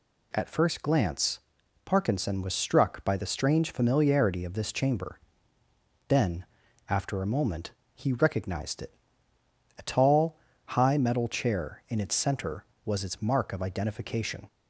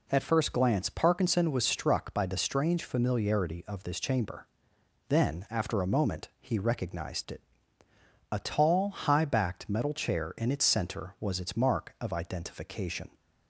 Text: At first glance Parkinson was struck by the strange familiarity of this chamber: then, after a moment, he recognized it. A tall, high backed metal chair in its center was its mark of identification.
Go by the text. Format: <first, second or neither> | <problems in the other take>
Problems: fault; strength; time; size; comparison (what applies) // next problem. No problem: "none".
second | pauses between "glance" and "Parkinson"; at 1.3 s; 0.44 s long // skips "backed"; at 10.9 s